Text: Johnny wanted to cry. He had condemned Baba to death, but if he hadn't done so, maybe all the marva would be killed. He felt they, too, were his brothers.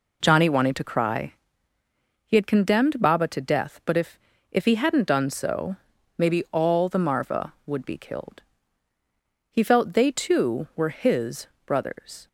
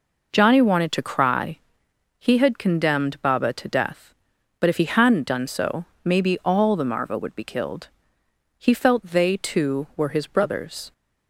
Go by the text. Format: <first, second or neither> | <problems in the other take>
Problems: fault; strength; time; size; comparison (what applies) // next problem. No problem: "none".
second | says "if" twice; at 4.5 s // pauses between "his" and "brothers"; slight; at 11.4 s; 0.18 s long